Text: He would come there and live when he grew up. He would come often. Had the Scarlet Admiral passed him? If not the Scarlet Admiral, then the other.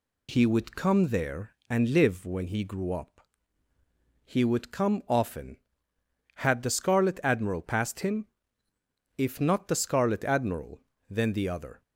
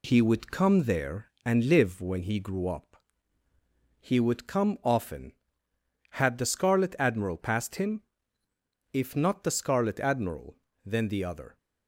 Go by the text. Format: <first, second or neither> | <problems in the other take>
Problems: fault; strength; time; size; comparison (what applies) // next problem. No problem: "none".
first | gets quieter; slight; throughout; 3.5 dB